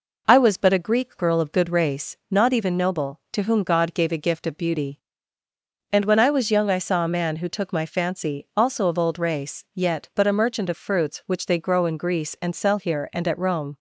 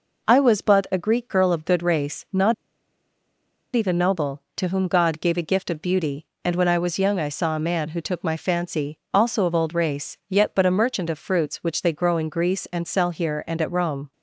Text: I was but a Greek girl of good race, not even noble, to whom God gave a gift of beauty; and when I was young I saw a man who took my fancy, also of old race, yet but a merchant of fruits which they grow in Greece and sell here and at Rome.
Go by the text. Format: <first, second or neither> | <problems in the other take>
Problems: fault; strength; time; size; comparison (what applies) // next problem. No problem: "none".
first | pauses between "not" and "even"; at 2.5 s; 1.1 s long